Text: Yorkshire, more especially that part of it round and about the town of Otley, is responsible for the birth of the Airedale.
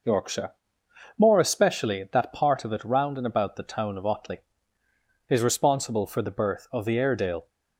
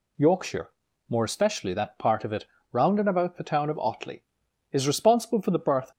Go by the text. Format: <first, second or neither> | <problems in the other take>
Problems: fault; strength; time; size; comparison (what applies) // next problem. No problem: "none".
first | pauses between "it" and "round"; slight; at 2.4 s; 0.26 s long // stops before "of the Airedale"; at 5.9 s